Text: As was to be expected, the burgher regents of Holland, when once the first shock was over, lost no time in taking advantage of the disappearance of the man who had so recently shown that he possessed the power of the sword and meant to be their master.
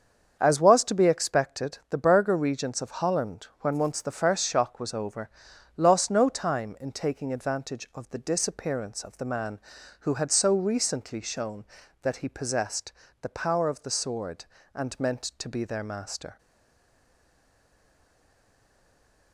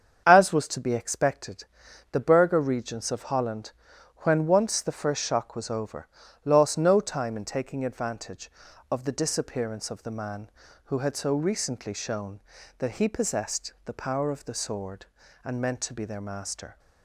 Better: second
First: starts louder than the rest; until 1.4 s; 7 dB // pauses between "possessed" and "the"; slight; at 12.9 s; 0.30 s long // stays silent after the last word; strong; from 16.3 s on; 3.0 s long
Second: starts louder than the rest; strong; until 1.2 s; 7.5 dB

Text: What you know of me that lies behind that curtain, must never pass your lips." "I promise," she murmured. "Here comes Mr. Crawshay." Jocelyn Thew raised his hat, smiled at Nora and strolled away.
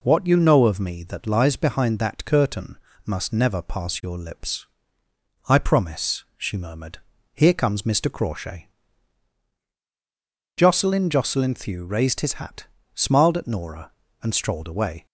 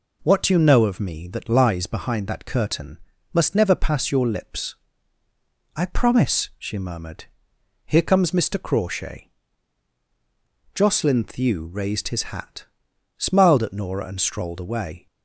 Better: second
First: says "Jocelyn" twice; at 11.0 s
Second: none

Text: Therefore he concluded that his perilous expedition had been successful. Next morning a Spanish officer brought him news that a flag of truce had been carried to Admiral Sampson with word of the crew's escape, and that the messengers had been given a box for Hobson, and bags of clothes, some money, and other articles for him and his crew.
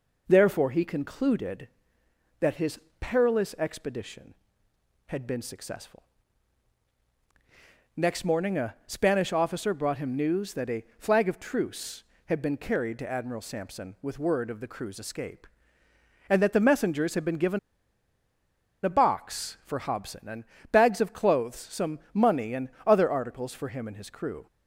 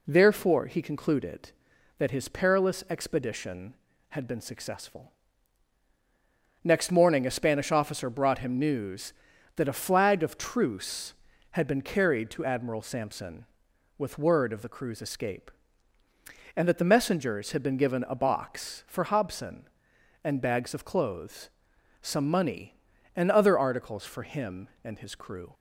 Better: second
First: pauses between "his" and "perilous"; slight; at 2.7 s; 0.22 s long // pauses between "a" and "flag"; slight; at 10.8 s; 0.16 s long // pauses between "given" and "a"; strong; at 17.5 s; 1.2 s long // pauses between "and" and "bags"; slight; at 20.4 s; 0.26 s long // pauses between "and" and "other"; slight; at 22.6 s; 0.18 s long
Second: none

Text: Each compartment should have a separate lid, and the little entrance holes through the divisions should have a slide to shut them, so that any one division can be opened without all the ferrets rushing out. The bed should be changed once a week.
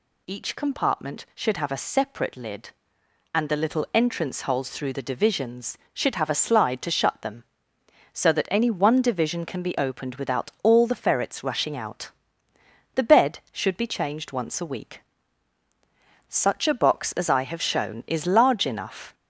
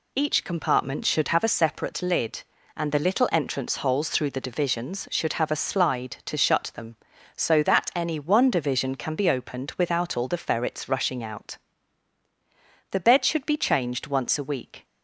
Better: second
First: goes on to say "Such a box as I have shown is large enough"; strong; from 16.2 s on; 2.8 s long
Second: none

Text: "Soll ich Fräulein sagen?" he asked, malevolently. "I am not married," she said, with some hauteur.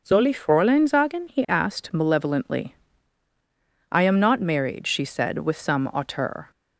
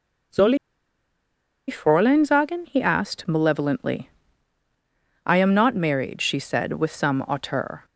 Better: first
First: none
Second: pauses between "Soll" and "ich"; at 0.5 s; 1.1 s long

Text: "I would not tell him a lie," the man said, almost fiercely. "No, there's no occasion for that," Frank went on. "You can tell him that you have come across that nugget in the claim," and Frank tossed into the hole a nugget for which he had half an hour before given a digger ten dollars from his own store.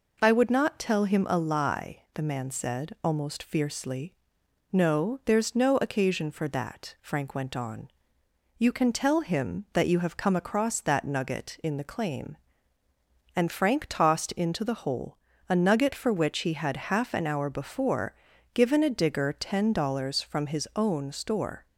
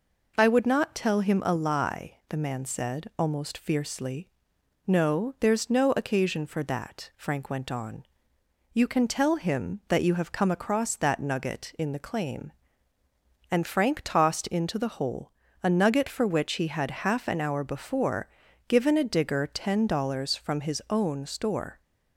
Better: neither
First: pauses between "hole" and "a"; slight; at 15.1 s; 0.30 s long // pauses between "before" and "given"; at 18.1 s; 0.40 s long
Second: pauses between "hole" and "a"; slight; at 15.3 s; 0.30 s long // pauses between "before" and "given"; at 18.2 s; 0.40 s long

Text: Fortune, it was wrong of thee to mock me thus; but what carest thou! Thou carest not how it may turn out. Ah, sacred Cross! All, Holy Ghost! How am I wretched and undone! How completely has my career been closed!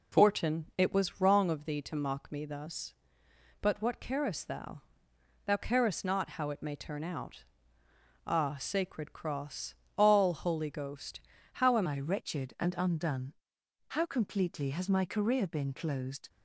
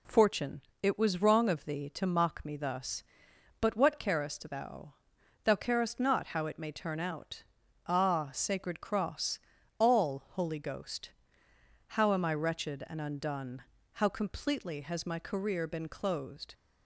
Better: second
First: changes voice at "I"; from 11.8 s on; 4.4 s long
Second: none

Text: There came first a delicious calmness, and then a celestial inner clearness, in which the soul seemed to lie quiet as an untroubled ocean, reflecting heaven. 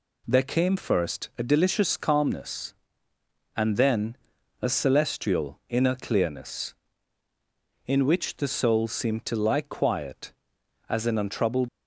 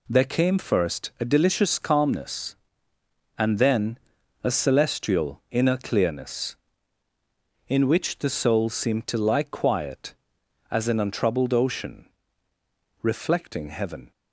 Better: second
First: pauses between "then" and "a"; at 4.1 s; 0.42 s long // stops before "ocean reflecting heaven"; at 11.6 s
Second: pauses between "then" and "a"; at 3.9 s; 0.42 s long

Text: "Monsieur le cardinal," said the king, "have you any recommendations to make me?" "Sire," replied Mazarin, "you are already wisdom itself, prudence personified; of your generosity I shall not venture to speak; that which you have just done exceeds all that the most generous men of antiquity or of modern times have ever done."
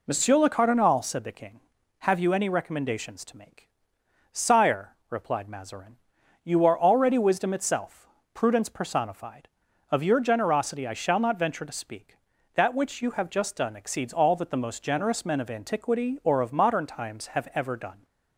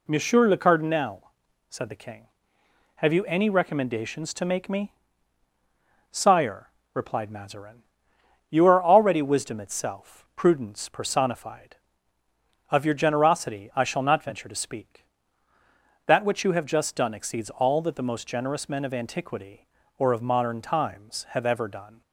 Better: second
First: skips "me"; at 4.0 s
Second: none

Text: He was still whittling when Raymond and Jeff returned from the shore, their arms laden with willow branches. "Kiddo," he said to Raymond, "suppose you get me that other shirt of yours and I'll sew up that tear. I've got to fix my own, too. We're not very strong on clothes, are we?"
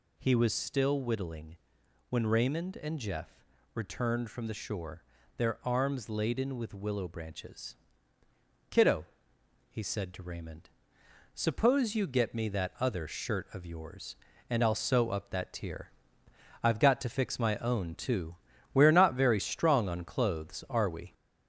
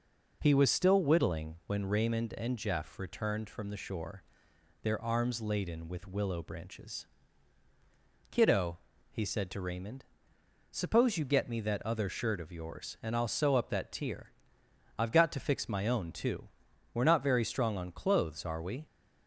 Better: second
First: gets louder; slight; throughout; 3.5 dB // pauses between "whittling" and "when"; noticeable; at 1.5 s; 0.52 s long // pauses between "Jeff" and "returned"; slight; at 3.4 s; 0.32 s long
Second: none

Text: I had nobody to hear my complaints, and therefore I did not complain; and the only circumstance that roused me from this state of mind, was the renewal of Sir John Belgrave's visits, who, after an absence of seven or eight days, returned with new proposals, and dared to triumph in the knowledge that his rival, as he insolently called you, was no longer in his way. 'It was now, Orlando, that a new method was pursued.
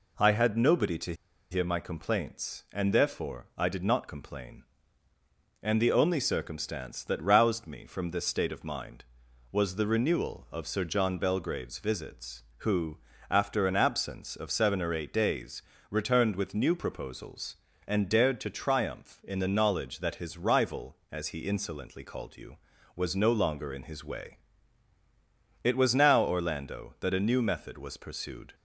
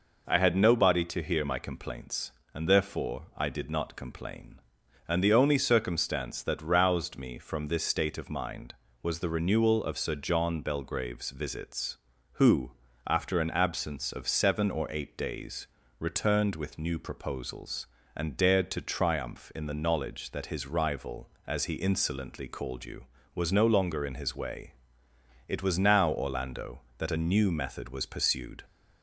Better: second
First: pauses between "to" and "hear"; at 1.1 s; 0.37 s long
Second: none

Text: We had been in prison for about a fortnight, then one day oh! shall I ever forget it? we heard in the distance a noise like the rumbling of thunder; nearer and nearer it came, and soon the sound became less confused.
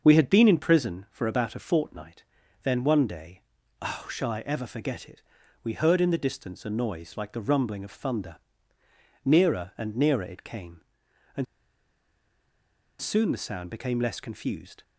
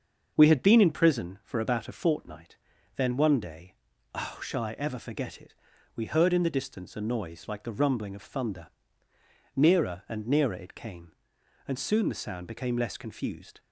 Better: second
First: starts louder than the rest; until 1.0 s; 6.5 dB // pauses between "day" and "oh"; at 3.4 s; 0.40 s long // pauses between "and" and "soon"; strong; at 11.4 s; 1.5 s long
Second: starts louder than the rest; until 1.3 s; 6.5 dB // pauses between "day" and "oh"; at 3.7 s; 0.40 s long

